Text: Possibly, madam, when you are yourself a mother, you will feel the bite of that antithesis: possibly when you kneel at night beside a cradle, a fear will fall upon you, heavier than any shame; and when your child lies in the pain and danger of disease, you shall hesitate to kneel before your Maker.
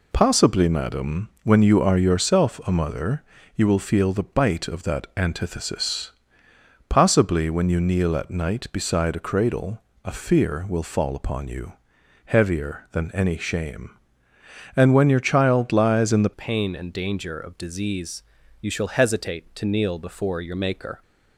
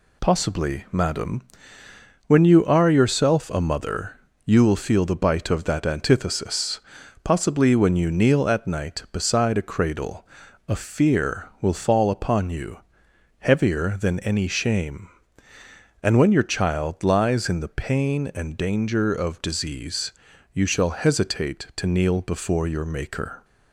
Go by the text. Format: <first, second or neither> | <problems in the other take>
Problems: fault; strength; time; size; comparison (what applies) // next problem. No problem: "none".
second | changes voice at "pain"; from 16.3 s on; 4.7 s long